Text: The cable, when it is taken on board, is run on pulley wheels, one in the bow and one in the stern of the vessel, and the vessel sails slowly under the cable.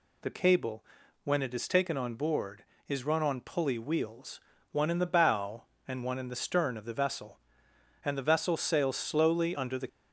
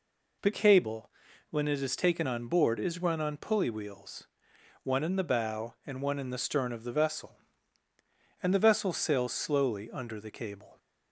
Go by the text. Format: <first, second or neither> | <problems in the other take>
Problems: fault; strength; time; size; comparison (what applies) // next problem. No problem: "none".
second | stops before "cable"; at 9.8 s